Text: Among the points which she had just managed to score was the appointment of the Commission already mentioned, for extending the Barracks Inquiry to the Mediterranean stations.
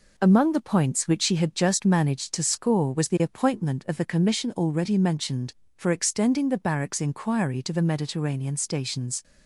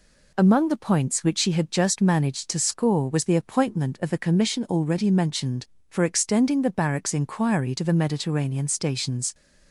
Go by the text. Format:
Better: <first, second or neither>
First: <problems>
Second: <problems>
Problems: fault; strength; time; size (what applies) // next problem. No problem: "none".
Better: second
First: gets quieter; throughout; 3.5 dB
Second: none